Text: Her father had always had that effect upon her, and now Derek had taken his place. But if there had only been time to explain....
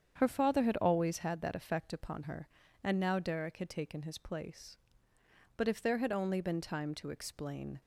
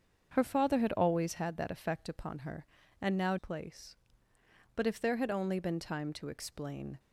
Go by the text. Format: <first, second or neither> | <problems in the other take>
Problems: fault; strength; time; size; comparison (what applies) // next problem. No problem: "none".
first | starts louder than the rest; until 1.3 s; 7 dB; strong in the first // skips "Derek had taken his"; at 3.3 s